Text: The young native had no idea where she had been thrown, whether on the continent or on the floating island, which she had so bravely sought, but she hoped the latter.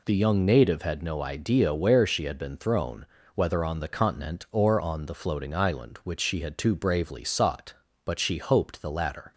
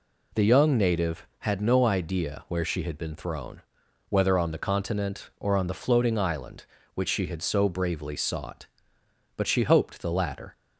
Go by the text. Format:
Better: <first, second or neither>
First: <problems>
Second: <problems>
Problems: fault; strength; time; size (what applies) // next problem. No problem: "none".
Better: second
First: says "too" for "so"; at 6.5 s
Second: none